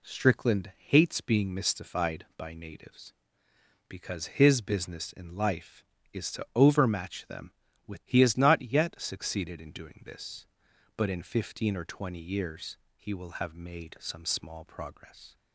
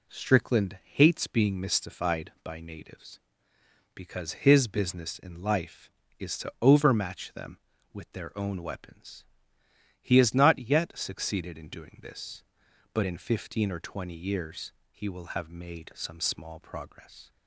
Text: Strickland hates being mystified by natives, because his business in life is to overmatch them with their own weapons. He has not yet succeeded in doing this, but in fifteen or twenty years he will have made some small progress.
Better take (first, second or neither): second